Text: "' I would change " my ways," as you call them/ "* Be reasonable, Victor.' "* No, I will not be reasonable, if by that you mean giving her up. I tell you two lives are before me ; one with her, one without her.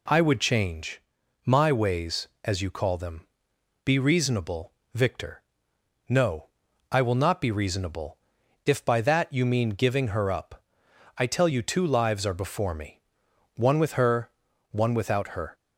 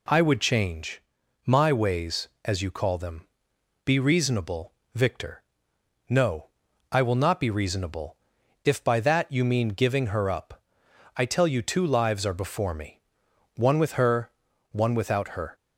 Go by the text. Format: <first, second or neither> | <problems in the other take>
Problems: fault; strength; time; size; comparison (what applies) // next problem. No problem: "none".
neither | none